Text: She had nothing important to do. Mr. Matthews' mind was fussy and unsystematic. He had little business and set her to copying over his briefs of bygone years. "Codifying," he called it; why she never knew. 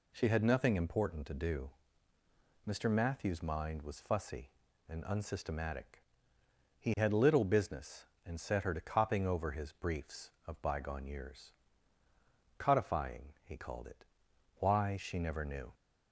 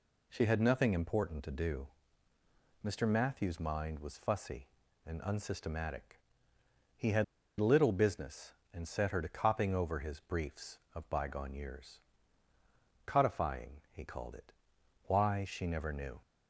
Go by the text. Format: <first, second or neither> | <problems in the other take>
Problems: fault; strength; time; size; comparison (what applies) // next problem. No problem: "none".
first | pauses between "had" and "little"; slight; at 7.2 s; 0.34 s long